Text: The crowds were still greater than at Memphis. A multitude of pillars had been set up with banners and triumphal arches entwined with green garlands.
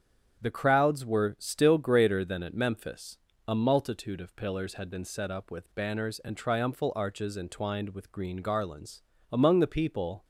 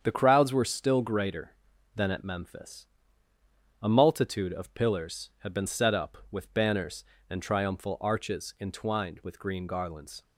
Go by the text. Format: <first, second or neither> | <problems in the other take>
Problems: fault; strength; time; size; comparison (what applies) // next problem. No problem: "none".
second | starts louder than the rest; strong; until 1.4 s; 8.5 dB; strong in the second // goes on to say "Among the people"; noticeable; from 9.3 s on; 0.92 s long